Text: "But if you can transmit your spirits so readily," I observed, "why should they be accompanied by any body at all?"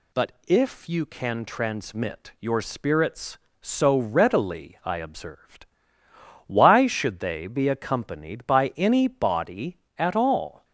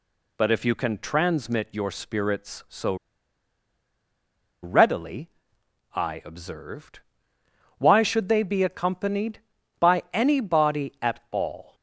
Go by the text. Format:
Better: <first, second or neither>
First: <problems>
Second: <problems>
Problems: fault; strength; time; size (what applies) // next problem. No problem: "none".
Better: first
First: none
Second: pauses between "so" and "readily"; strong; at 2.9 s; 1.6 s long